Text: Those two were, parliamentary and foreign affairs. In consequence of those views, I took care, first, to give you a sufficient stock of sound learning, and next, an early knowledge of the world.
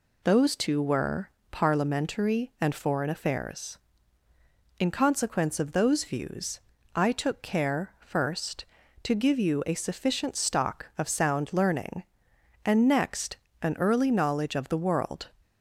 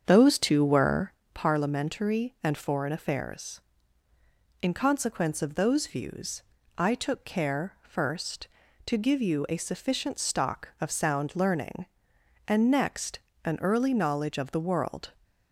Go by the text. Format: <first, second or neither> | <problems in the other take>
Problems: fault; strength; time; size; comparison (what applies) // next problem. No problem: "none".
first | starts louder than the rest; strong; until 1.2 s; 7.5 dB